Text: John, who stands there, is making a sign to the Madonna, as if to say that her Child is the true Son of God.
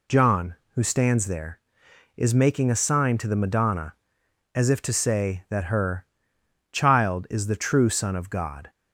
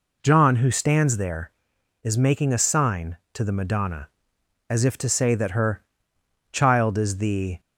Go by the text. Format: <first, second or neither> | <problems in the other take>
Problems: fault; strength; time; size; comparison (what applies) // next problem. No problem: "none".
first | pauses between "her" and "Child"; noticeable; at 5.8 s; 0.70 s long; noticeable in the first // stops before "true Son of God"; at 7.5 s